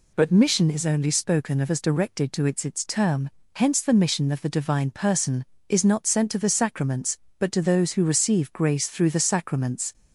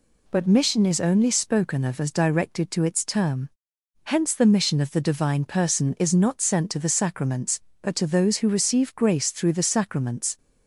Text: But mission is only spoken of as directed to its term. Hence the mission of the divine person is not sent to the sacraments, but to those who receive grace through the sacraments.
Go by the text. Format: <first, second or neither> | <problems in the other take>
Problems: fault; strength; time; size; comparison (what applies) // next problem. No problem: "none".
second | says "its" twice; at 2.6 s